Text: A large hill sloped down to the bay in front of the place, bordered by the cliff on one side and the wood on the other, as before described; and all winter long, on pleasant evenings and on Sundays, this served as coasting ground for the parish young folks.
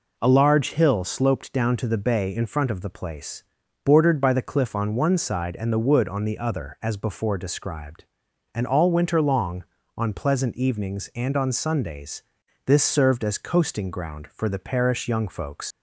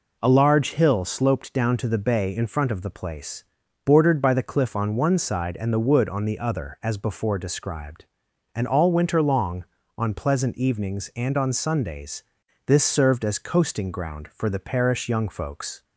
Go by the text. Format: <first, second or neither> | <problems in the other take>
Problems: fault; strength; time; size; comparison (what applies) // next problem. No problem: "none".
second | leaves "folks" unfinished; at 15.7 s; 130 ms